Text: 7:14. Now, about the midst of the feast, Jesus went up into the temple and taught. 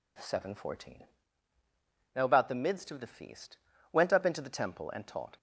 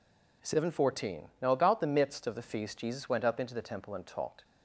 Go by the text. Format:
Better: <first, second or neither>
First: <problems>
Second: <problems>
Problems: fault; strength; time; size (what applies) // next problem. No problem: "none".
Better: second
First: skips "Jesus"; at 3.7 s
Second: none